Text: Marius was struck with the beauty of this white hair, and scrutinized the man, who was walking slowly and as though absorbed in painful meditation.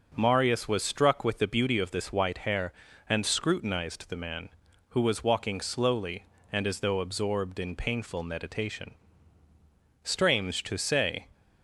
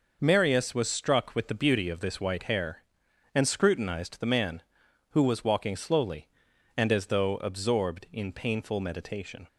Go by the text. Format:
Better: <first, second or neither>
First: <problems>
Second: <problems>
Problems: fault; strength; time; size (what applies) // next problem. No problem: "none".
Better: second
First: starts louder than the rest; until 1.1 s; 6 dB // goes on to say "Strange to say"; noticeable; from 10.0 s on; 1.2 s long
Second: none